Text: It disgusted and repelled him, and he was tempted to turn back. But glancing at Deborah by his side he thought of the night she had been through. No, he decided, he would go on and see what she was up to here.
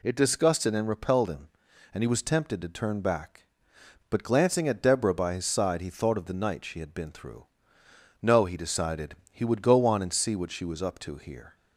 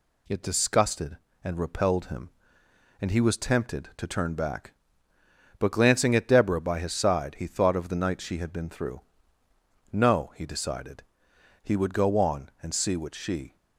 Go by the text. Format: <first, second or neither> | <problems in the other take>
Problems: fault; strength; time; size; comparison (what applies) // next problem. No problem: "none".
first | stops before "was up to here"; at 13.5 s